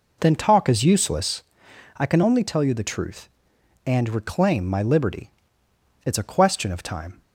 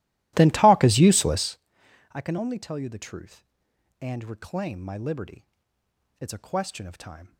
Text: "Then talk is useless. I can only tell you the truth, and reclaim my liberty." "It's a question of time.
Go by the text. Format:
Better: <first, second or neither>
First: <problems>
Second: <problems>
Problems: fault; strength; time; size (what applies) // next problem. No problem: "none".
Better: first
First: none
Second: starts louder than the rest; strong; until 1.6 s; 16 dB